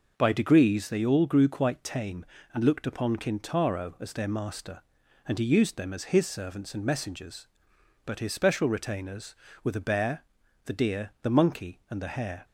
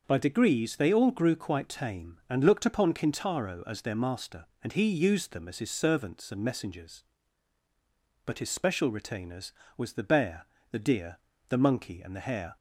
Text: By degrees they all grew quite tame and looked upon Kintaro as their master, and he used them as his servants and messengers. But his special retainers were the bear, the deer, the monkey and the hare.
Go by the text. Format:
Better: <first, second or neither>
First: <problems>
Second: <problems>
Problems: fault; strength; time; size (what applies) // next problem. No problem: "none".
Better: first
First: none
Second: says "was" for "were"; at 9.7 s